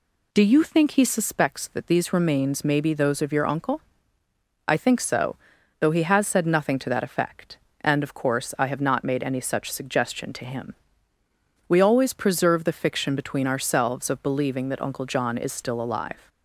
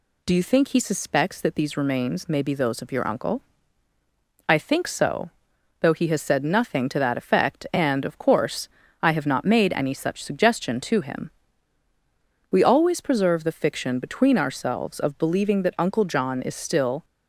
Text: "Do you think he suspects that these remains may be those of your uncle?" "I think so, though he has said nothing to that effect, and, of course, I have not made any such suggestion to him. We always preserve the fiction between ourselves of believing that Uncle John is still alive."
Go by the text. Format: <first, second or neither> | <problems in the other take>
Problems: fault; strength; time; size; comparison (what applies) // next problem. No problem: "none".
first | stops before "alive"; at 17.0 s